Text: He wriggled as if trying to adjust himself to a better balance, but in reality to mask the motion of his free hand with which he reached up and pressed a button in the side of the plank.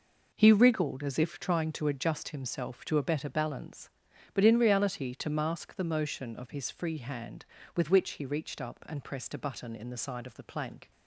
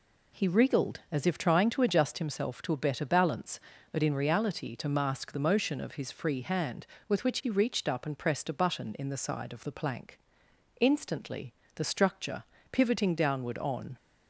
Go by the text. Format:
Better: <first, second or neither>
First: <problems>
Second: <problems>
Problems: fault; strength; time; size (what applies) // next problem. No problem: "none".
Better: first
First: none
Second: goes on to say "Instantly the structure pivoting downward on"; strong; from 10.7 s on; 3.1 s long